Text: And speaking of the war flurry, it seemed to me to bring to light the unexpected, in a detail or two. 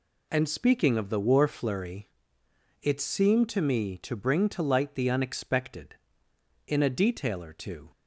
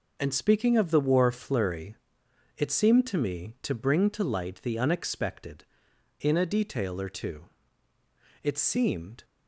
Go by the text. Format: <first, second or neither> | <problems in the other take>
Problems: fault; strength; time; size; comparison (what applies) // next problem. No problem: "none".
first | goes on to say "It seemed"; noticeable; from 8.4 s on; 0.80 s long